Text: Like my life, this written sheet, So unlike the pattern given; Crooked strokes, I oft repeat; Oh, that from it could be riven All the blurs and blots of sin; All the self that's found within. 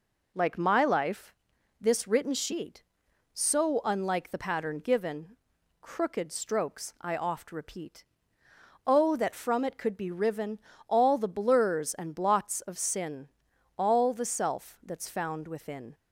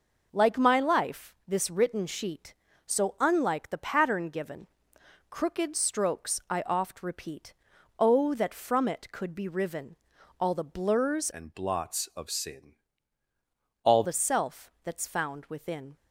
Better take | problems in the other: first | pauses between "riven" and "All"; at 9.9 s; 0.44 s long; slight in the first // changes voice from "and" to "All"; from 11.3 to 14.0 s; 2.7 s long

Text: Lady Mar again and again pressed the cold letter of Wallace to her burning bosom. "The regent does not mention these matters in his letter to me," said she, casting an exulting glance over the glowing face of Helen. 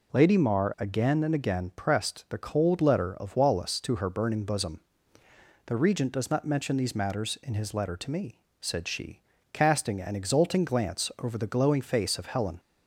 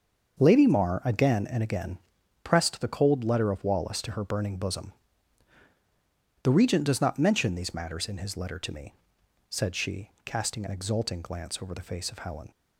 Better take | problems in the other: first | starts louder than the rest; until 1.4 s; 6.5 dB // pauses between "again" and "pressed"; noticeable; at 1.9 s; 0.46 s long // skips "glowing"; at 11.8 s

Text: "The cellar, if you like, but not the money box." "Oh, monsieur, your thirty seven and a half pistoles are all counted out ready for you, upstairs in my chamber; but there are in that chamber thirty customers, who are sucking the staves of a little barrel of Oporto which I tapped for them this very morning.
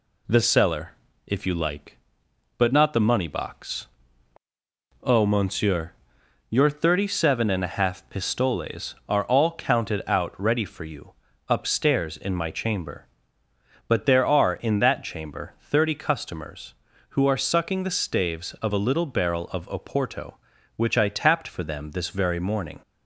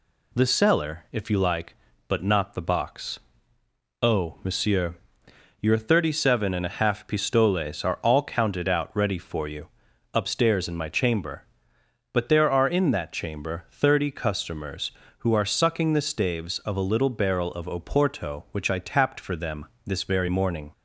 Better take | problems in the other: first | skips "money"; at 2.6 s // pauses between "them" and "this"; slight; at 19.6 s; 0.18 s long

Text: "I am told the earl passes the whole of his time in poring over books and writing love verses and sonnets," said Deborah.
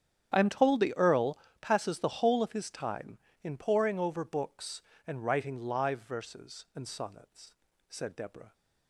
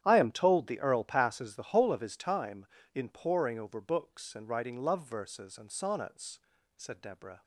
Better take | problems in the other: second | starts louder than the rest; strong; until 1.3 s; 9 dB; strong in the second // pauses between "earl" and "passes"; slight; at 1.3 s; 0.24 s long // says "live" for "love"; at 5.6 s

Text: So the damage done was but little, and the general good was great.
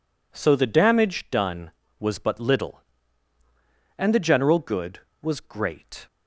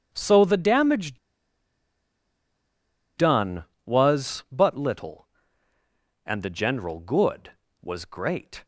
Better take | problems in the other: first | pauses between "damage" and "done"; strong; at 1.1 s; 1.9 s long

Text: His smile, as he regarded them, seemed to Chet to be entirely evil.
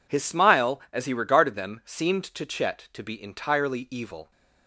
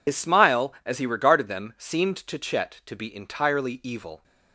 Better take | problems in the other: first | loses the start of "His"; at 0.0 s; 60 ms

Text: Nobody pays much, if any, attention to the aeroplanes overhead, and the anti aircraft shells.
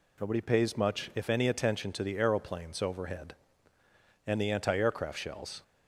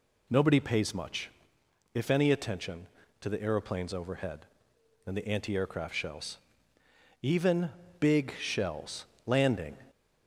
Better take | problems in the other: first | goes on to say "Even big shells landing"; strong; from 7.2 s on; 2.5 s long

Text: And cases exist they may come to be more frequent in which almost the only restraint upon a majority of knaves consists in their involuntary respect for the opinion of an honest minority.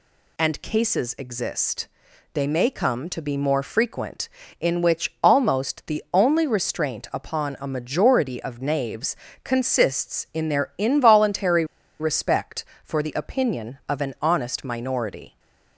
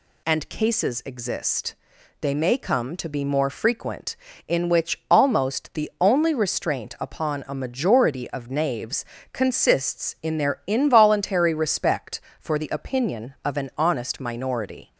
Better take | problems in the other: second | pauses between "exist" and "they"; noticeable; at 1.8 s; 0.46 s long; noticeable in the second // pauses between "knaves" and "consists"; slight; at 9.1 s; 0.26 s long; slight in the second // pauses between "involuntary" and "respect"; slight; at 11.6 s; 0.35 s long

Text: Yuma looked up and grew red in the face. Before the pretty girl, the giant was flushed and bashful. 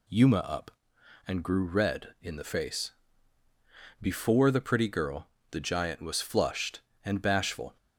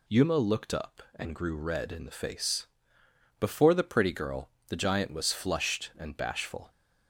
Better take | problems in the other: second | skips "looked"; at 0.3 s

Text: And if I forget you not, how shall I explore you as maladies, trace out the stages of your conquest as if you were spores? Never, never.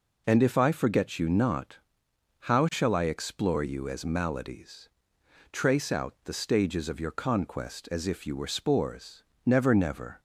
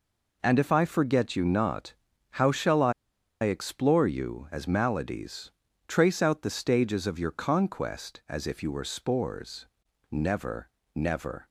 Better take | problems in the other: first | pauses between "I" and "explore"; noticeable; at 2.9 s; 0.51 s long

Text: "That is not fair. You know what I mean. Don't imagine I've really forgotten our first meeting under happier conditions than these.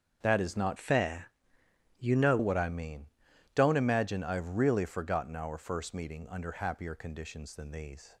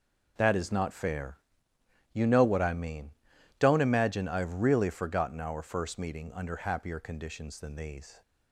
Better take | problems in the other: second | starts louder than the rest; strong; until 1.2 s; 7 dB // changes voice from "fair" to "know"; from 0.7 to 2.3 s; 1.6 s long

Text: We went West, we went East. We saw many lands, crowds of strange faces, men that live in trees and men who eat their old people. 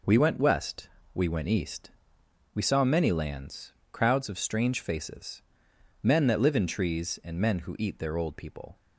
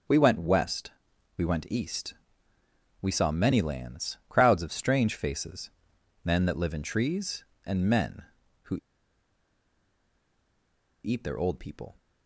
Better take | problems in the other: first | starts louder than the rest; until 1.5 s; 6.5 dB // pauses between "who" and "eat"; strong; at 8.7 s; 2.2 s long

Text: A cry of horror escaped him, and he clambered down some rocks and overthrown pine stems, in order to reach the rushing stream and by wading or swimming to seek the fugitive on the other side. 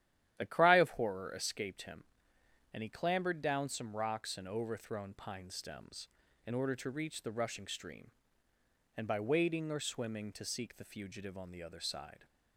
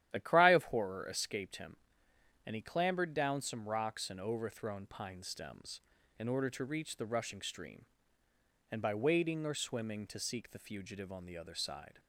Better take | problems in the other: neither | starts louder than the rest; strong; the same in both

